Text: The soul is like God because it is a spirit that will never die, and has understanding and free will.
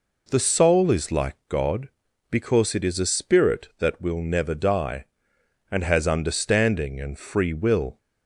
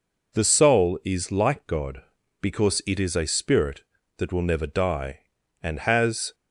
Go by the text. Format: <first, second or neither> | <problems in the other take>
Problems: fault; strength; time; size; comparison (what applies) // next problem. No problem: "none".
first | stops before "understanding and free will"; at 6.3 s